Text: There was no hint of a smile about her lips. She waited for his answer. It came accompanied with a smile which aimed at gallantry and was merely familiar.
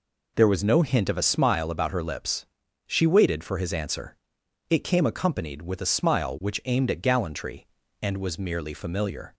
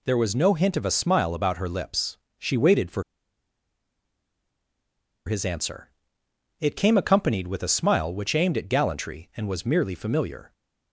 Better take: first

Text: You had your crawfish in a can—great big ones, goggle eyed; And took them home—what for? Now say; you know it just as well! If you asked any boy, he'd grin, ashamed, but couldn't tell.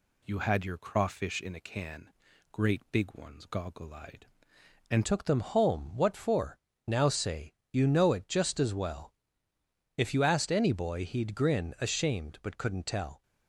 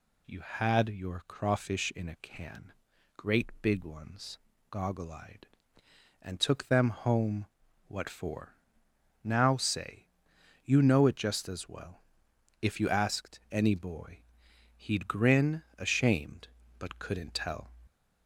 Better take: second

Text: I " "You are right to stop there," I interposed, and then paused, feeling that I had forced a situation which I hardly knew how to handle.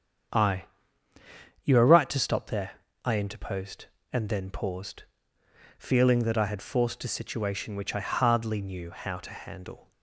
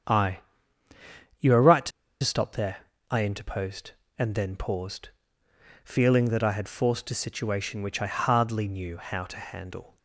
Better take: first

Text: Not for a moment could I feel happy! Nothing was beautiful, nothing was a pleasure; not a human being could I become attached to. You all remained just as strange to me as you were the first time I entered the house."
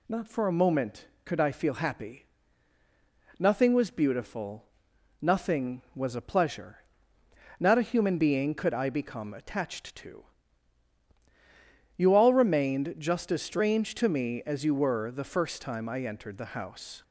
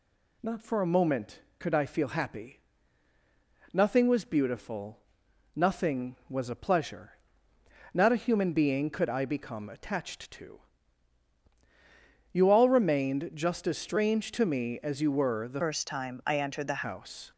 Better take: first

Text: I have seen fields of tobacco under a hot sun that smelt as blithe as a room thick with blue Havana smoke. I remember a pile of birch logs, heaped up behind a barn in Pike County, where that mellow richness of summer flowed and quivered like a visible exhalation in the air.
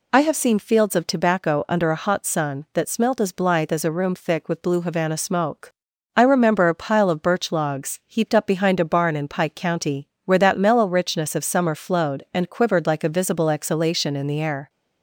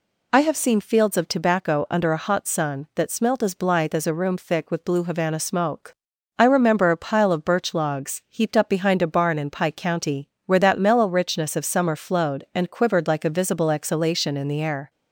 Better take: neither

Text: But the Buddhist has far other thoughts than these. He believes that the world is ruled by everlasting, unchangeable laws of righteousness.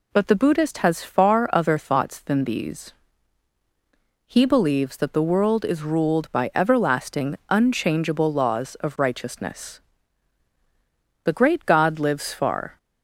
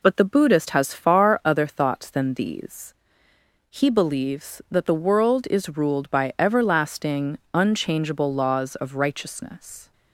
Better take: second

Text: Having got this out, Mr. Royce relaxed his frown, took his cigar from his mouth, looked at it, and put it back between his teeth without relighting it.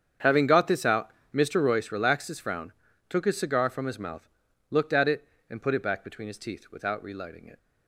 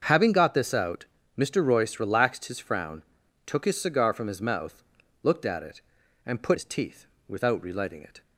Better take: first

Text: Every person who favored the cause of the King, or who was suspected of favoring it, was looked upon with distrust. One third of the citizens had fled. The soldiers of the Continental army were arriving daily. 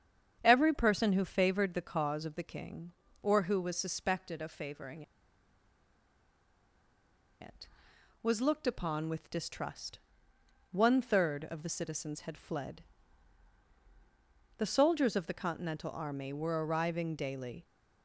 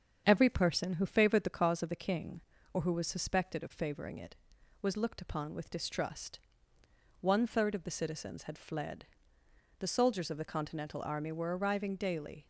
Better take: second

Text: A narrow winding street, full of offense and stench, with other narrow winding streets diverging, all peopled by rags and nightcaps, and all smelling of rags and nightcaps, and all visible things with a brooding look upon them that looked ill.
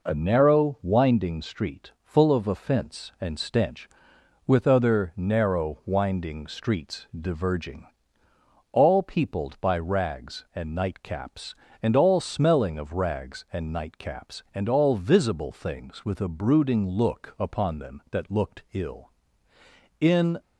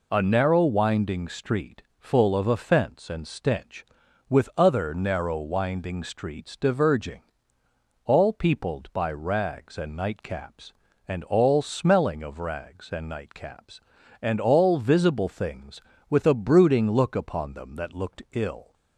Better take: second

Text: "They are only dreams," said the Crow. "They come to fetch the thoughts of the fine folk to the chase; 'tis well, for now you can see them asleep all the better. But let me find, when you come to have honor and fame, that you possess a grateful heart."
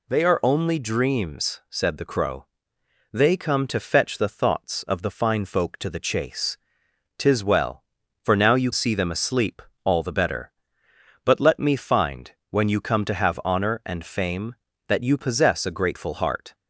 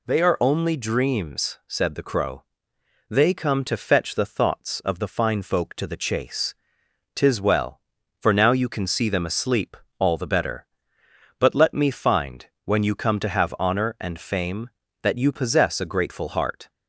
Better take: second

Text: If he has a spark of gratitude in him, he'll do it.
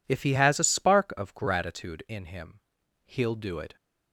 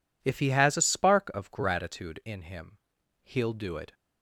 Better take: neither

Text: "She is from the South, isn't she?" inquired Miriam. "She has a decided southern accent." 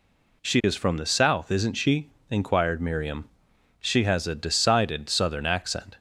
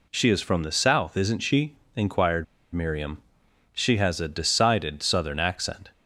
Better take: first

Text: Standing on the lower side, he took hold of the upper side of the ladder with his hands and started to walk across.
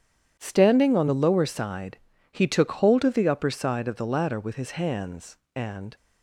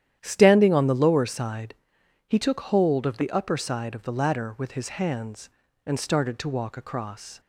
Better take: second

